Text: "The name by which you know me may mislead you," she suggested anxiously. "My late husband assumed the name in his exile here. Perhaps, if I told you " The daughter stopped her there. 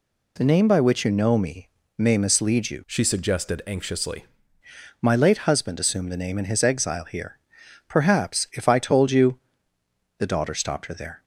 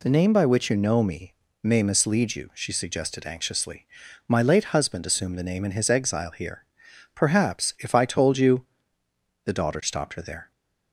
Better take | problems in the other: second | pauses between "me" and "may"; slight; at 1.6 s; 0.28 s long; slight in the second // changes voice from "she" to "anxiously"; from 2.8 to 4.2 s; 1.4 s long

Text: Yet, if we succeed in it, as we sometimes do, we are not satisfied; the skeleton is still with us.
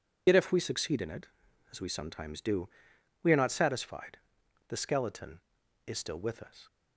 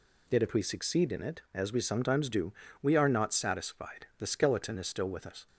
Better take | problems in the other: second | loses the start of "Yet"; at 0.2 s; 65 ms

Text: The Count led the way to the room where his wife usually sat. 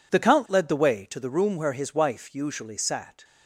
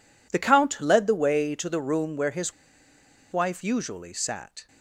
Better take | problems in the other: first | pauses between "his" and "wife"; noticeable; at 2.5 s; 0.79 s long

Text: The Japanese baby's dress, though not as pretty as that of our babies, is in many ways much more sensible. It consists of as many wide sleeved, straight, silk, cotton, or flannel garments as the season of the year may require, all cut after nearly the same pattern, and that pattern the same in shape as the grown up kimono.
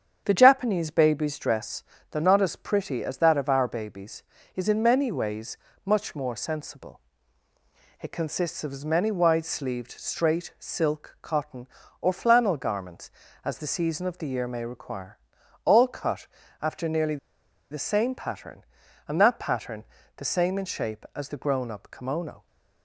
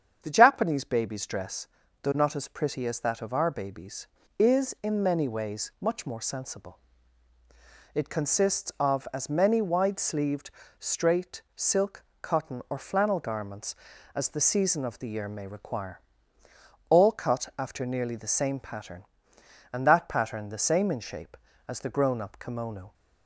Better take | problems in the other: second | starts louder than the rest; strong; until 1.2 s; 8 dB; strong in the second // pauses between "ways" and "much"; slight; at 5.5 s; 0.26 s long // pauses between "cut" and "after"; slight; at 16.2 s; 0.36 s long // pauses between "nearly" and "the"; noticeable; at 17.1 s; 0.54 s long // pauses between "pattern" and "the"; slight; at 19.8 s; 0.32 s long

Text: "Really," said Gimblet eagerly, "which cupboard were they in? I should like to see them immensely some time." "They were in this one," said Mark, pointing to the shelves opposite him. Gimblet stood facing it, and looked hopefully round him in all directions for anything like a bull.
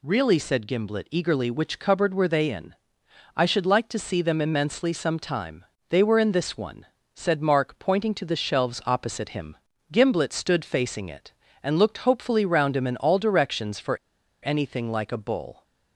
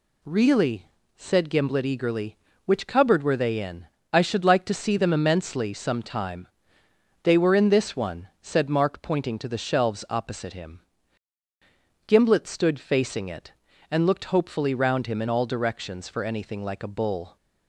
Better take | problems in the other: second | pauses between "for" and "anything"; noticeable; at 13.9 s; 0.46 s long

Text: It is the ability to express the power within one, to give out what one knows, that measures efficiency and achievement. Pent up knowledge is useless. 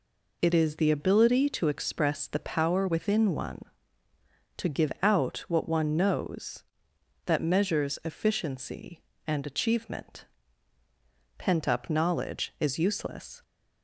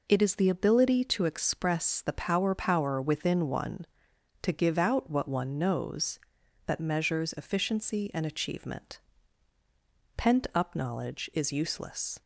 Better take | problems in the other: first | says "power" twice; at 2.5 s

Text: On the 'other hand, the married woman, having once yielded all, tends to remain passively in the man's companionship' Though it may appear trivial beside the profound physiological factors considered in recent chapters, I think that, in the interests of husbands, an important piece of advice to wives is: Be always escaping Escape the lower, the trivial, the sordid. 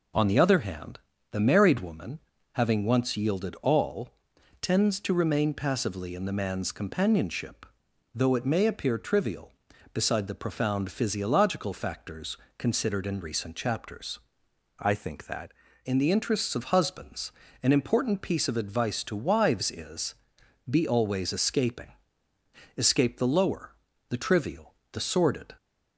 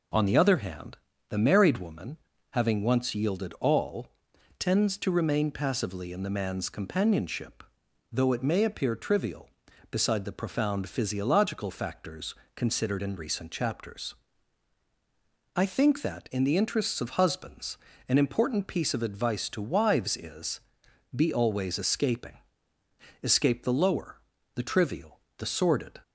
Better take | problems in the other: second | pauses between "companionship" and "Though"; noticeable; at 7.6 s; 0.50 s long; noticeable in the second // pauses between "factors" and "considered"; slight; at 12.3 s; 0.22 s long; slight in the second // changes voice from "I" to "that"; from 14.8 to 15.5 s; 0.7 s long // pauses between "escaping" and "Escape"; noticeable; at 21.9 s; 0.84 s long; noticeable in the second

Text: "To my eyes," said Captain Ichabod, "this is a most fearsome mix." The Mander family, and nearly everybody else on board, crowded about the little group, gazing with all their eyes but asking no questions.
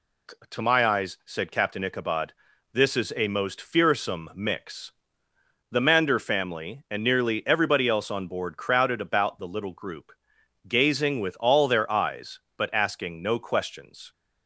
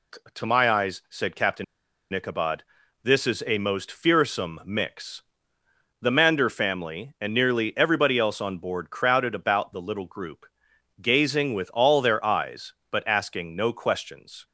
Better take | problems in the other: first | pauses between "Captain" and "Ichabod"; noticeable; at 1.6 s; 0.48 s long

